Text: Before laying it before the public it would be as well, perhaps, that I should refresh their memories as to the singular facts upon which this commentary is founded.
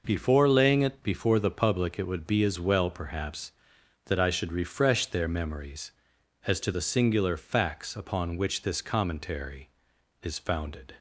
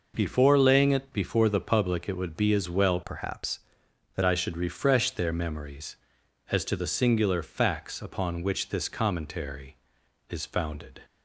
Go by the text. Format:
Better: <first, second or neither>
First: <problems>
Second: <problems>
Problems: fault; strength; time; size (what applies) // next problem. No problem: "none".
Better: first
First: none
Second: changes voice from "perhaps" to "that"; from 3.0 to 4.2 s; 1.2 s long